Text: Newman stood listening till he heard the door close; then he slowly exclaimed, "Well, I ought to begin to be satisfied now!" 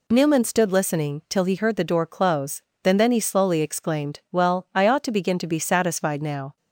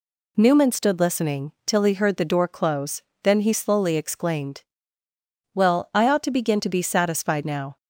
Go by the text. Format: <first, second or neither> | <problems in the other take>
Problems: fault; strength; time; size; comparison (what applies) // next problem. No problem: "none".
second | says "then" twice; at 2.9 s